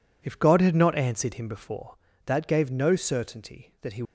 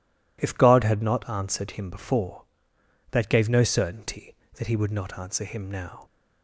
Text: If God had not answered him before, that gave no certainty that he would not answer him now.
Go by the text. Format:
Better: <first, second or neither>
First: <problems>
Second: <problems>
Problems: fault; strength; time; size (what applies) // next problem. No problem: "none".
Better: second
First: stops before "would not answer him now"; at 4.0 s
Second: none